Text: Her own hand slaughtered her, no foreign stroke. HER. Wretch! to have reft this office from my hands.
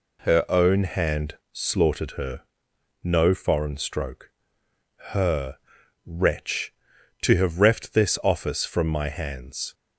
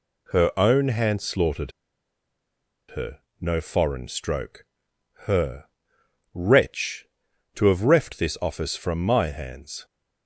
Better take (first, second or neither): first